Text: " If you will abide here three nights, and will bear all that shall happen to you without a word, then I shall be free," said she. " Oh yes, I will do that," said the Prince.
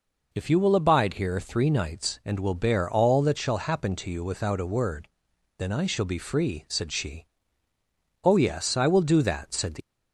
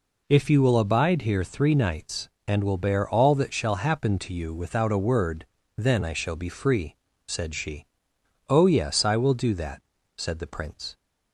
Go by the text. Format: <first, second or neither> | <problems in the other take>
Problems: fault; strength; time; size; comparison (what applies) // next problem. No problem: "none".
second | stops before "Prince"; at 9.8 s